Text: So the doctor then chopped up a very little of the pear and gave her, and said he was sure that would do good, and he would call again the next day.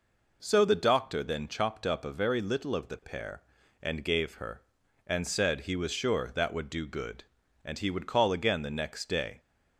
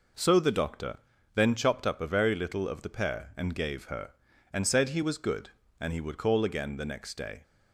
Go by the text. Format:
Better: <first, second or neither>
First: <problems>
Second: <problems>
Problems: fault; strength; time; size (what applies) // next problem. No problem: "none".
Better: first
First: none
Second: pauses between "doctor" and "then"; slight; at 0.9 s; 0.36 s long // skips "sure that would do"; at 5.1 s